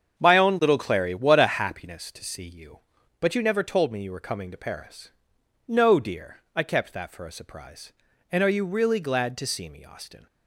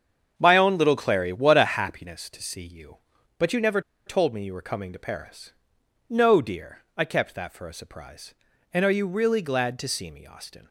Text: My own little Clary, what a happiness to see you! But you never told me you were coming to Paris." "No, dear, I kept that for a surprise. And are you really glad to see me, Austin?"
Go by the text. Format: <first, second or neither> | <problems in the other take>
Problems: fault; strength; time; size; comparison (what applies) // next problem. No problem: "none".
first | starts louder than the rest; strong; until 1.3 s; 7.5 dB; strong in the first // pauses between "never" and "told"; slight; at 3.8 s; 0.26 s long